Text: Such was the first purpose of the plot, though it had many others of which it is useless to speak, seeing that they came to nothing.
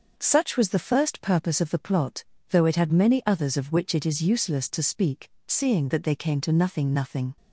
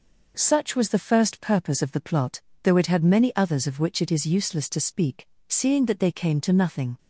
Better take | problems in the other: second | says "nothing" twice; at 6.9 s

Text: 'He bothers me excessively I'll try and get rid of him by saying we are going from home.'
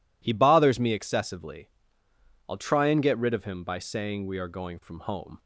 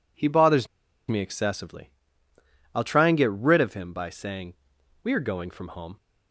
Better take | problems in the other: first | pauses between "bothers" and "me"; at 0.6 s; 0.41 s long // pauses between "excessively" and "I'll"; noticeable; at 1.9 s; 0.84 s long; noticeable in the first // pauses between "saying" and "we"; noticeable; at 4.5 s; 0.48 s long

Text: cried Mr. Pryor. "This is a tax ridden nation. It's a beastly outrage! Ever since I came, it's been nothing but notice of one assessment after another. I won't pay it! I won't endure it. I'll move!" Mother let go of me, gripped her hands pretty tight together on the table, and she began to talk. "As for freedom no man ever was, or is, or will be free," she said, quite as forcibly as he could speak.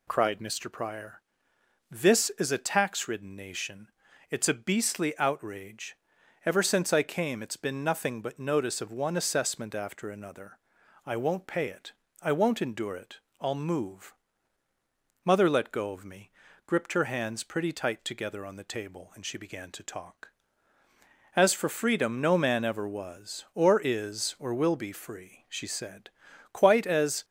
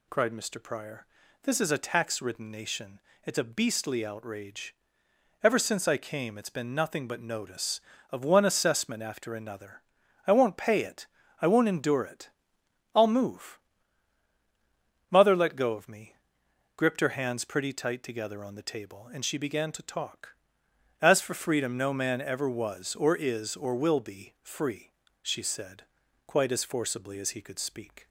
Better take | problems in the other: second | stops before "forcibly as he could speak"; at 27.2 s

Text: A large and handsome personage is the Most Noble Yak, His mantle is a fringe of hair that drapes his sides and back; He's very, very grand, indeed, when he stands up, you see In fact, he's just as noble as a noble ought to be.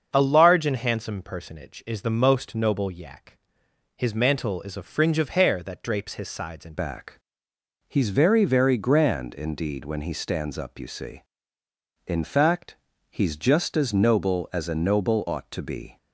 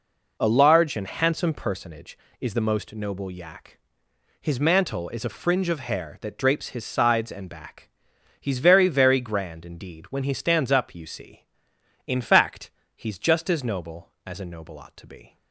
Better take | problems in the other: second | starts louder than the rest; until 1.1 s; 7 dB // changes voice at "back"; from 6.7 s on; 9.2 s long

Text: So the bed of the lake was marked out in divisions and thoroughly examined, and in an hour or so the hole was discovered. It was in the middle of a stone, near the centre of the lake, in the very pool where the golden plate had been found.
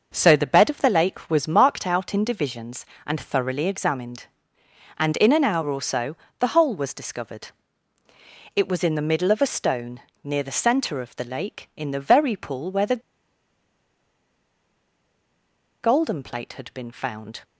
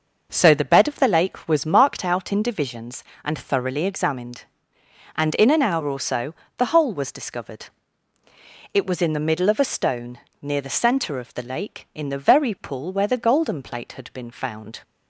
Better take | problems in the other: second | starts louder than the rest; noticeable; until 1.1 s; 6 dB; noticeable in the second // pauses between "so" and "the"; slight; at 6.1 s; 0.22 s long; slight in the second // pauses between "the" and "golden"; strong; at 13.0 s; 2.8 s long

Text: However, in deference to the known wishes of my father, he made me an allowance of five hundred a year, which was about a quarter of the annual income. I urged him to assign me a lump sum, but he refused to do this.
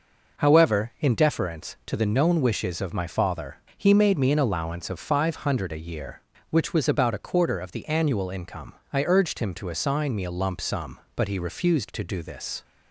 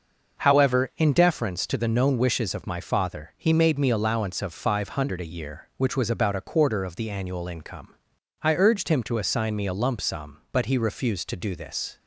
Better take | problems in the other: first | starts louder than the rest; noticeable; until 1.4 s; 6 dB // skips "an"; at 3.9 s

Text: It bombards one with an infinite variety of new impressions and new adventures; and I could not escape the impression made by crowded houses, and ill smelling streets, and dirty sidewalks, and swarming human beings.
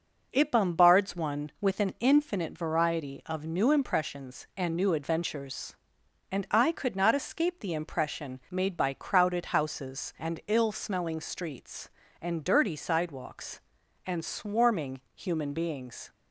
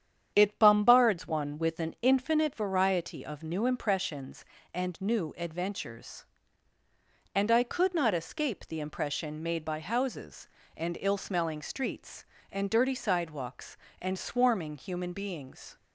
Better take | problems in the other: first | starts louder than the rest; strong; until 1.3 s; 9 dB // skips "crowded"; at 9.7 s

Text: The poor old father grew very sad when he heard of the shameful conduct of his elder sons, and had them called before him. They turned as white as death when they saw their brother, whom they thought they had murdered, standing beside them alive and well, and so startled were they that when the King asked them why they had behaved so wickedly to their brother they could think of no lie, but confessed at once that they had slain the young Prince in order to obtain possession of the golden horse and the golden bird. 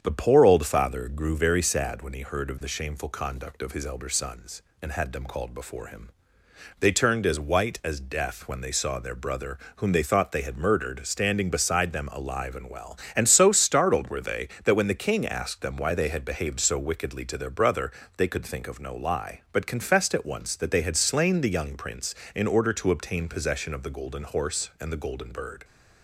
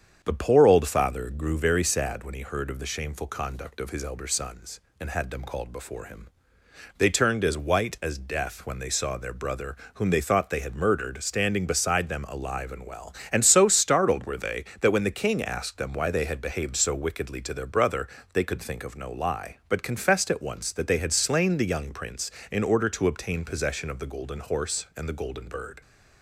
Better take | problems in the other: neither | starts louder than the rest; strong; the same in both // pauses between "brother" and "they"; slight; the same in both

